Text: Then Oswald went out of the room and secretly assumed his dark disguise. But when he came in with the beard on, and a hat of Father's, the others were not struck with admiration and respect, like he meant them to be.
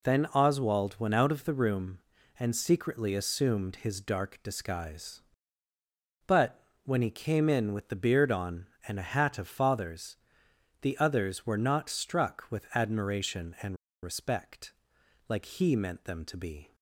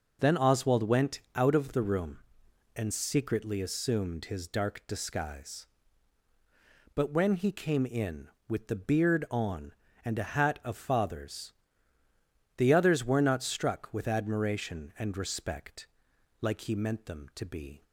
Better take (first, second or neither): second